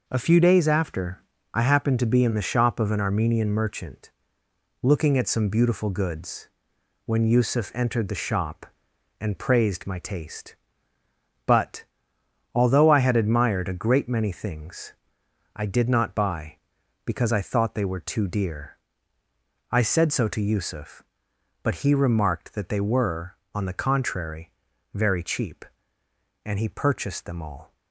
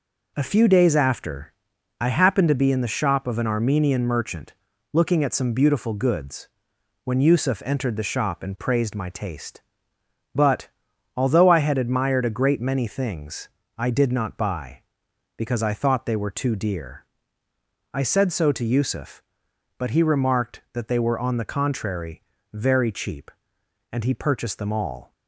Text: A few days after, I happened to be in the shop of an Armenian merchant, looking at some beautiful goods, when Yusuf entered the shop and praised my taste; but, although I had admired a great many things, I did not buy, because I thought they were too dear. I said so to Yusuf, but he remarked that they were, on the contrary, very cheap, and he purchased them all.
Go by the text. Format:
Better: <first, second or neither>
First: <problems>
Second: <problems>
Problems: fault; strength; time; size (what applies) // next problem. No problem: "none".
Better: neither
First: none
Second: none